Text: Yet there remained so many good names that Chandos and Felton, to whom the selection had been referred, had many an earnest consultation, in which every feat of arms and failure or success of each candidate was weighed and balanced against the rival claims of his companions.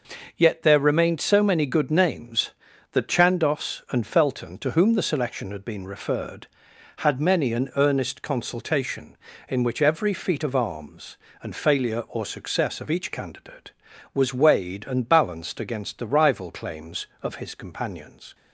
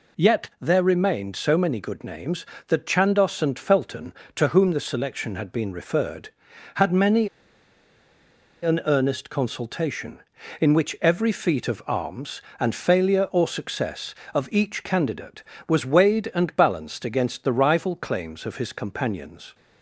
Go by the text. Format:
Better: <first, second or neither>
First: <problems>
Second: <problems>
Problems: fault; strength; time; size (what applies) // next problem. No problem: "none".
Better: first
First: none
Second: pauses between "many" and "an"; strong; at 7.2 s; 1.3 s long